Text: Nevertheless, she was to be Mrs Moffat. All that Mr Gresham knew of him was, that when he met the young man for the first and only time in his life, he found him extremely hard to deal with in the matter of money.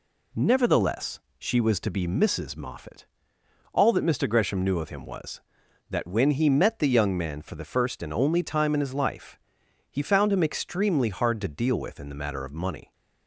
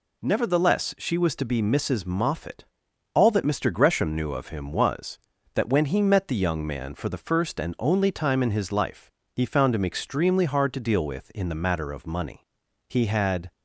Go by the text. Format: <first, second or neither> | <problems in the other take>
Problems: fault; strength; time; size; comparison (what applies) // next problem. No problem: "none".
first | goes on to say "He had"; noticeable; from 12.8 s on; 0.62 s long